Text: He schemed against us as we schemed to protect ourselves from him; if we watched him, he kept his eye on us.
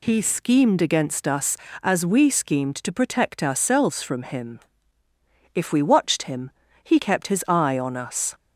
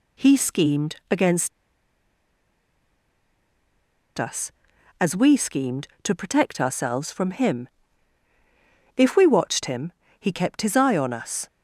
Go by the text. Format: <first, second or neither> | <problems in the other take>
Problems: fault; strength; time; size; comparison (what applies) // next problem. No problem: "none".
first | pauses between "schemed" and "against"; slight; at 0.9 s; 0.16 s long // pauses between "against" and "us"; strong; at 1.5 s; 2.6 s long